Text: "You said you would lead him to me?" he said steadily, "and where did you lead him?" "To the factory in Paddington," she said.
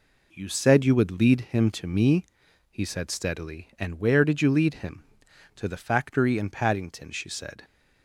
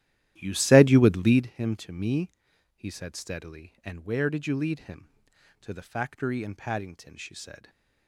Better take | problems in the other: first | starts louder than the rest; strong; until 1.5 s; 13 dB

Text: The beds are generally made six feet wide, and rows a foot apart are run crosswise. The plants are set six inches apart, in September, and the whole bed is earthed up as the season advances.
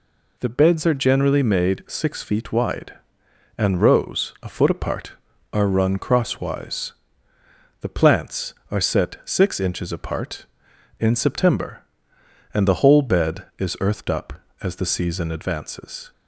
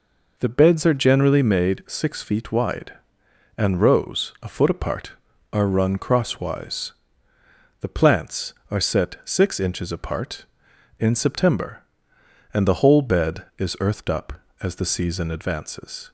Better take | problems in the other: first | starts louder than the rest; noticeable; until 1.7 s; 5 dB

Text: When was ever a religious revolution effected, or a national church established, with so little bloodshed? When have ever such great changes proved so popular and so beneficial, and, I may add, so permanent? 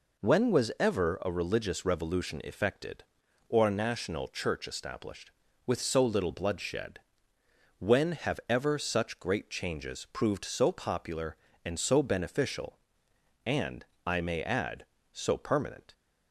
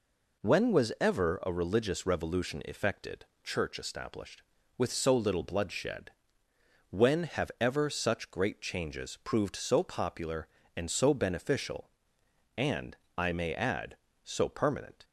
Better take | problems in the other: first | skips "or a national"; at 3.3 s

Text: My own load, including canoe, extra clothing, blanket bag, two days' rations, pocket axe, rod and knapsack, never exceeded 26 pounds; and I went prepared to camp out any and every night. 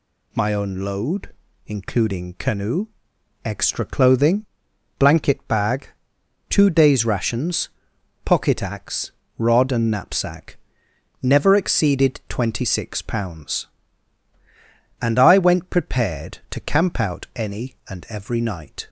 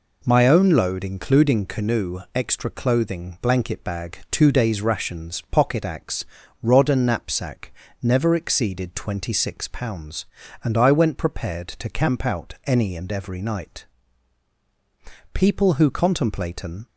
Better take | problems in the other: first | goes on to say "People who contemplate an"; from 15.3 s on; 1.5 s long

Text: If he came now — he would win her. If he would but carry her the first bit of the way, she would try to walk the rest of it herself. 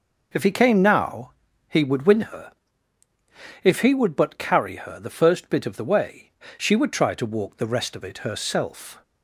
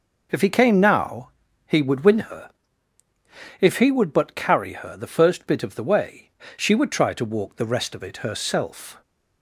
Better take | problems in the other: neither | none

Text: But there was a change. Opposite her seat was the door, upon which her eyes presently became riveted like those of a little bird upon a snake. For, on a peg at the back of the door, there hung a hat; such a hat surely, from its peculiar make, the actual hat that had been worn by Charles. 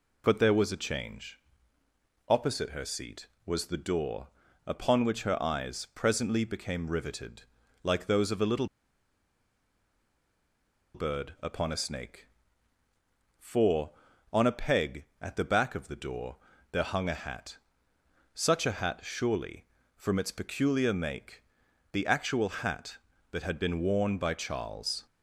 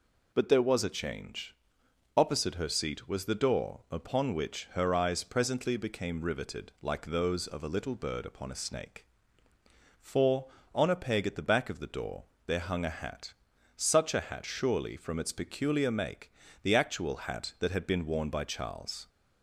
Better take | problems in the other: second | pauses between "riveted" and "like"; at 7.4 s; 0.40 s long // pauses between "little" and "bird"; strong; at 8.6 s; 2.2 s long

